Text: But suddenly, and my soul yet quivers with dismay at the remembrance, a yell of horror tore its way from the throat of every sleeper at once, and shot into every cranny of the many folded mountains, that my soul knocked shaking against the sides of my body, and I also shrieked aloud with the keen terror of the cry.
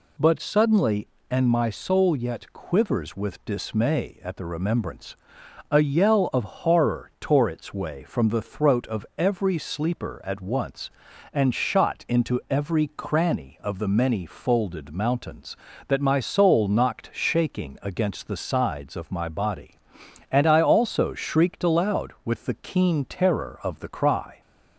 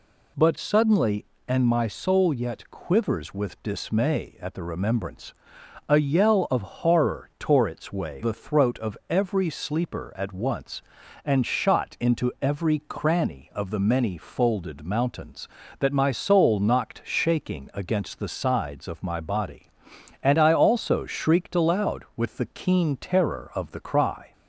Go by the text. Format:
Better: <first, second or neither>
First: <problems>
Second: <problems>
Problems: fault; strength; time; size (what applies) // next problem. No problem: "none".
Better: first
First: none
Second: skips "from"; at 8.2 s